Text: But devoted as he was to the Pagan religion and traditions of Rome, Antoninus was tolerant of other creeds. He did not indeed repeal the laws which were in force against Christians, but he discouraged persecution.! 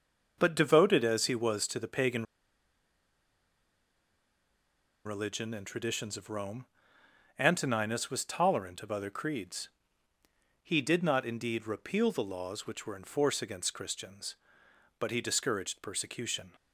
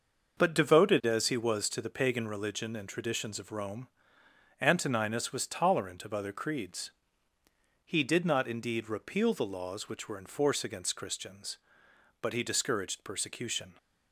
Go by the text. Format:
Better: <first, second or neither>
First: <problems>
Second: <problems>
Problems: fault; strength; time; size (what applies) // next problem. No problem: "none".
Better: second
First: starts louder than the rest; noticeable; until 1.3 s; 6 dB // pauses between "Pagan" and "religion"; strong; at 2.2 s; 2.8 s long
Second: starts louder than the rest; noticeable; until 1.4 s; 6 dB